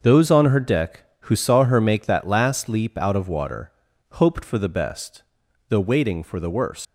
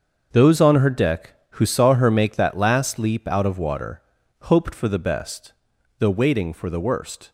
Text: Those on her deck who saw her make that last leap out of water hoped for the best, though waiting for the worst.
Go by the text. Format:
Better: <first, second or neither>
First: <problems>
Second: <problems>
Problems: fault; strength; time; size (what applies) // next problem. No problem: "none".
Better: second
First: starts louder than the rest; until 1.0 s; 6.5 dB // pauses between "water" and "hoped"; at 3.7 s; 0.42 s long // leaves "worst" unfinished; at 6.8 s; 165 ms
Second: starts louder than the rest; until 1.3 s; 7 dB // pauses between "water" and "hoped"; at 4.0 s; 0.42 s long